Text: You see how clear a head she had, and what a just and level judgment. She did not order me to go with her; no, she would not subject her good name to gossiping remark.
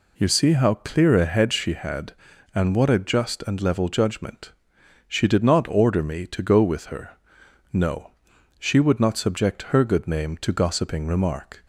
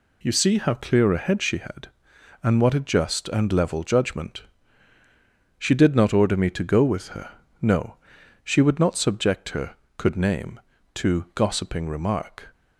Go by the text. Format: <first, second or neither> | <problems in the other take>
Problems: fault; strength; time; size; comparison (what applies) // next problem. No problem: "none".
first | says "could" for "good"; at 9.9 s